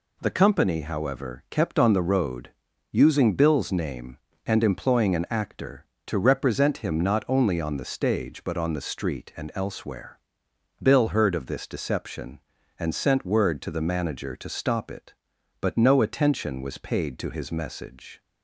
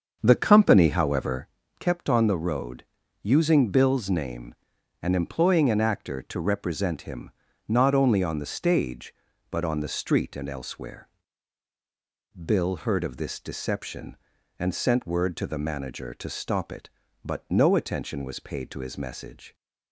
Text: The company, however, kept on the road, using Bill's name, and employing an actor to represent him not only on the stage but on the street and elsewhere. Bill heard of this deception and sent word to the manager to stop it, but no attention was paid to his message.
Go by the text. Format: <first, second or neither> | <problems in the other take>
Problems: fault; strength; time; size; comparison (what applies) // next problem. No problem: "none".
first | starts louder than the rest; until 1.5 s; 7 dB // pauses between "him" and "not"; at 7.3 s; 0.38 s long